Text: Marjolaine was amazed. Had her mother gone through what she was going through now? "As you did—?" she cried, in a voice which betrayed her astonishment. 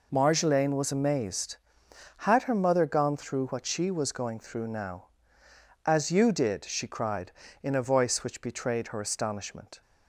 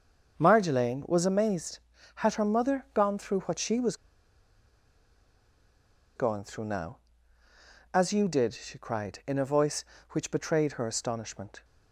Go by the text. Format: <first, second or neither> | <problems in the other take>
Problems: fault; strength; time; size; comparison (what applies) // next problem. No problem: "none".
first | starts louder than the rest; until 1.3 s; 6.5 dB // pauses between "was" and "going"; strong; at 3.9 s; 2.2 s long